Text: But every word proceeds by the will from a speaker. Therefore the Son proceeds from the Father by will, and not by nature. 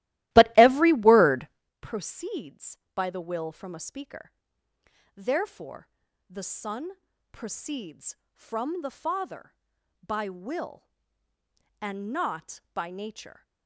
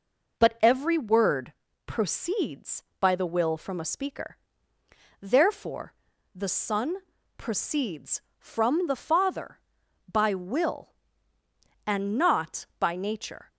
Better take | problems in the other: second | starts louder than the rest; strong; until 1.7 s; 16.5 dB // pauses between "word" and "proceeds"; slight; at 1.4 s; 0.34 s long; slight in the second // pauses between "Therefore" and "the"; at 5.8 s; 0.42 s long; also in the second // pauses between "Son" and "proceeds"; at 6.9 s; 0.40 s long; also in the second

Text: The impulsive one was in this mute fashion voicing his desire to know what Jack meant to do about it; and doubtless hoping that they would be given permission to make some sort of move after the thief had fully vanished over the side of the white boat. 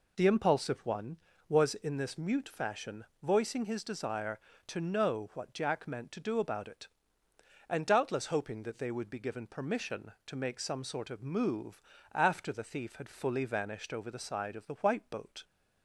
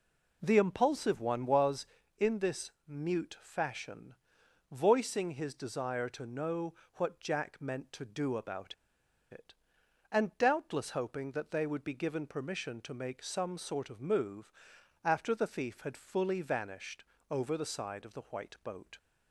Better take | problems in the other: first | pauses between "this" and "mute"; slight; at 2.7 s; 0.16 s long // pauses between "fashion" and "voicing"; noticeable; at 4.1 s; 0.56 s long; slight in the first // pauses between "know" and "what"; slight; at 6.7 s; 0.22 s long // pauses between "about" and "it"; noticeable; at 8.7 s; 0.56 s long // pauses between "move" and "after"; noticeable; at 14.5 s; 0.54 s long; slight in the first // pauses between "vanished" and "over"; slight; at 17.0 s; 0.26 s long

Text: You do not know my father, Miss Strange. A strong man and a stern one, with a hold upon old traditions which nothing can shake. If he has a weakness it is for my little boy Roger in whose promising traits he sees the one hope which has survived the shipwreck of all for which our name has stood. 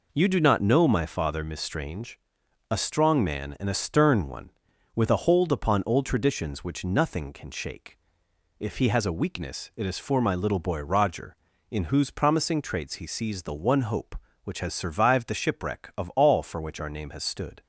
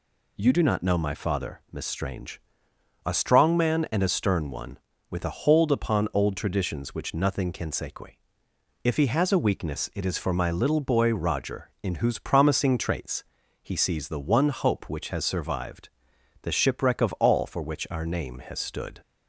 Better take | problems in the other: first | says "sequi" for "shake"; at 7.7 s // pauses between "traits" and "he"; at 13.2 s; 0.40 s long // pauses between "survived" and "the"; noticeable; at 15.8 s; 0.54 s long

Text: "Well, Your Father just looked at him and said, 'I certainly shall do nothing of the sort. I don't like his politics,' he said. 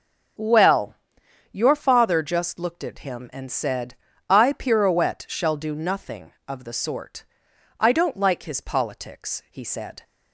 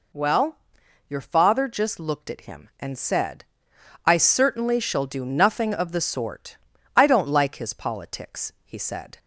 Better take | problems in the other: second | starts louder than the rest; until 1.9 s; 6 dB // says "pirouette" for "certainly"; at 4.5 s

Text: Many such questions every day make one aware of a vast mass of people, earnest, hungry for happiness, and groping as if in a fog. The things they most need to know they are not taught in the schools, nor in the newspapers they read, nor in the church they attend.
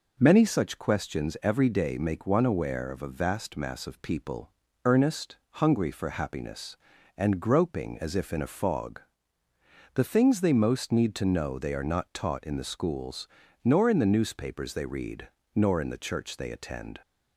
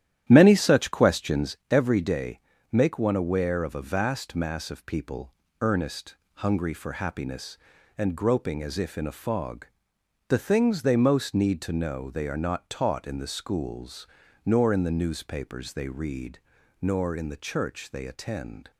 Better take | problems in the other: first | starts louder than the rest; strong; until 1.5 s; 11.5 dB // pauses between "day" and "make"; slight; at 2.3 s; 0.34 s long

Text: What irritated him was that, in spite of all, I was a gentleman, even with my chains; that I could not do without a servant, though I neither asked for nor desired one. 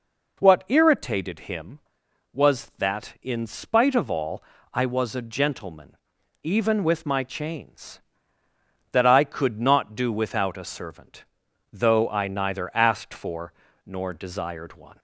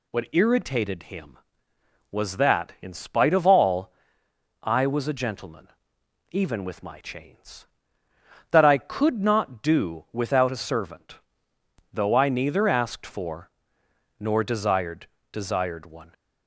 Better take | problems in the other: first | pauses between "for" and "nor"; noticeable; at 13.4 s; 0.68 s long; slight in the first // says "desired" twice; at 15.3 s

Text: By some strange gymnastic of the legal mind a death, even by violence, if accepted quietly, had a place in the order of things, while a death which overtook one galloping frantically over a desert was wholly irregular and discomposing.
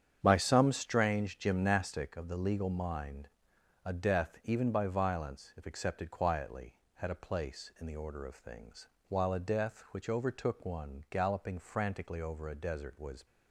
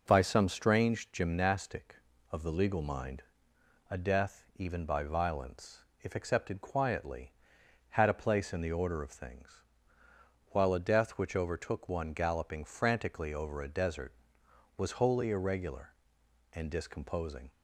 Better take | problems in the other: second | starts louder than the rest; strong; until 1.2 s; 8.5 dB // pauses between "mind" and "a"; noticeable; at 3.2 s; 0.58 s long; noticeable in the second // stops before "wholly irregular and discomposing"; at 13.2 s

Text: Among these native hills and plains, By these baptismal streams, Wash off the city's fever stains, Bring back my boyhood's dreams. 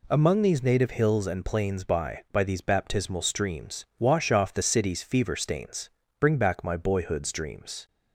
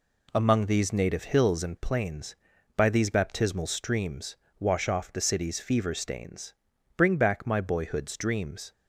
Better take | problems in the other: second | says "By" twice; at 2.2 s

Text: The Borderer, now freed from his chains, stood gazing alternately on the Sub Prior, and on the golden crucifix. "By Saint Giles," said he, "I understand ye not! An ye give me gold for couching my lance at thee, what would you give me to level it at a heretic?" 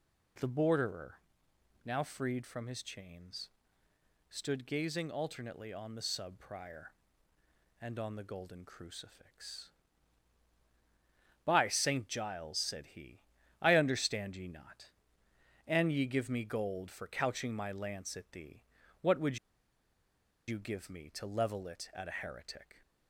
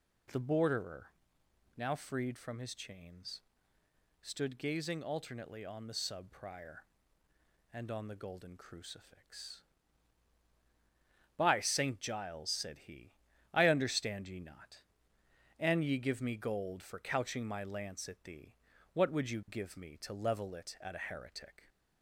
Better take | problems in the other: second | pauses between "would" and "you"; at 19.3 s; 1.0 s long

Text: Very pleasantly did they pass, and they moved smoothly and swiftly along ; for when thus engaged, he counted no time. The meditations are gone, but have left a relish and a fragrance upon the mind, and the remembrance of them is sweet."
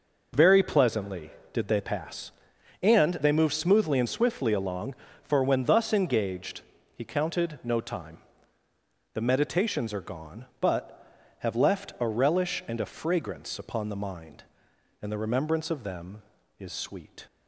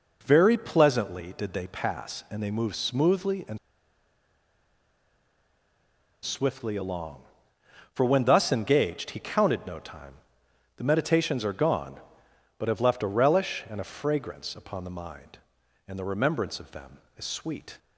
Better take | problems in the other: first | pauses between "and" and "swiftly"; strong; at 3.5 s; 2.6 s long

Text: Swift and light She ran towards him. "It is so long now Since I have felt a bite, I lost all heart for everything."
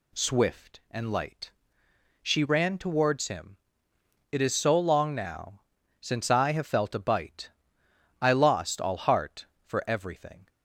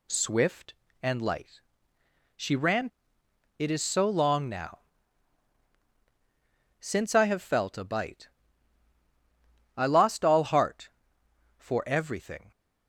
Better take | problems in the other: first | pauses between "light" and "She"; noticeable; at 1.5 s; 0.76 s long; noticeable in the first // skips "towards him"; at 3.2 s // pauses between "now" and "Since"; strong; at 4.8 s; 2.0 s long; also in the first

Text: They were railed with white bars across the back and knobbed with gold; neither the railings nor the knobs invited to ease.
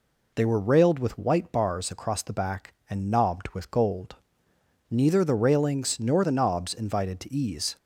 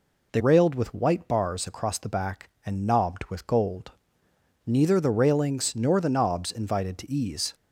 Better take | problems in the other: first | skips "were"; at 0.4 s

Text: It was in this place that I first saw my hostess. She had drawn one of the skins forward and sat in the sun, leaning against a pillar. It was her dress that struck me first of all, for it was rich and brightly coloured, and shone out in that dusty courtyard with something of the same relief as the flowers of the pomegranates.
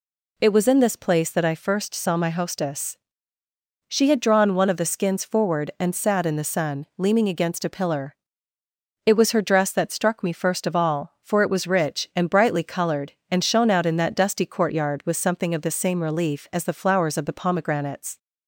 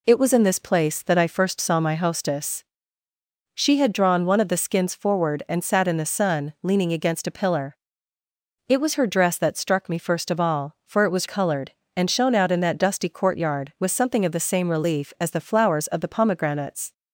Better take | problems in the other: first | skips "rich and brightly"; at 11.2 s

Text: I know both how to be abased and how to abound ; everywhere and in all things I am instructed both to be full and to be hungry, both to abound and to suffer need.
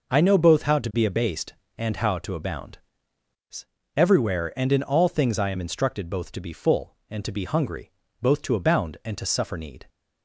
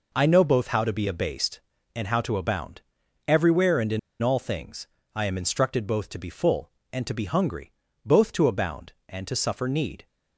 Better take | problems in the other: first | pauses between "in" and "all"; slight; at 3.9 s; 0.22 s long // pauses between "things" and "I"; slight; at 4.8 s; 0.28 s long

